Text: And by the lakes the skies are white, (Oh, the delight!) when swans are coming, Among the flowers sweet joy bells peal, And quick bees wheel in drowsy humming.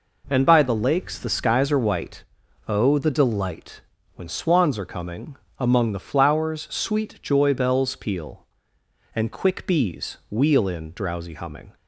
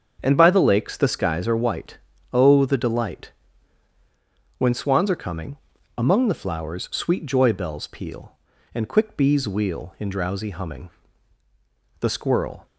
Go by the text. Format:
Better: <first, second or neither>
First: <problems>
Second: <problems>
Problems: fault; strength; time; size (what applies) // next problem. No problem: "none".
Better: first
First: none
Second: starts louder than the rest; until 1.2 s; 7 dB // goes on to say "The squirrel"; noticeable; from 12.0 s on; 0.64 s long